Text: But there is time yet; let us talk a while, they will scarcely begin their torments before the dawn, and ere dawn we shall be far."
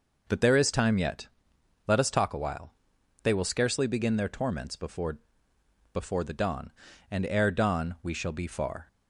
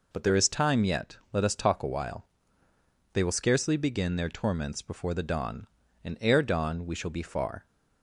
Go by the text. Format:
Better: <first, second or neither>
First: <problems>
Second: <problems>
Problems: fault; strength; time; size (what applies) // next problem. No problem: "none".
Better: second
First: says "before" twice; at 5.9 s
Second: none